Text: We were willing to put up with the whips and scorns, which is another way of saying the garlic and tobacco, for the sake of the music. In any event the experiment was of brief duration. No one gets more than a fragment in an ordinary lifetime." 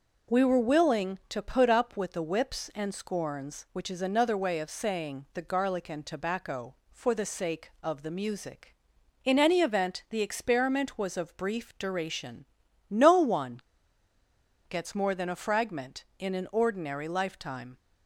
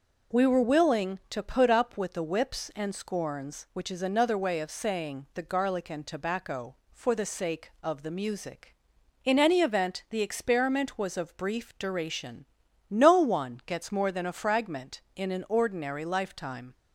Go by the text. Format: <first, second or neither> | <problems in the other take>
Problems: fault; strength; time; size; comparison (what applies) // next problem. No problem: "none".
second | pauses between "one" and "gets"; at 13.6 s; 1.0 s long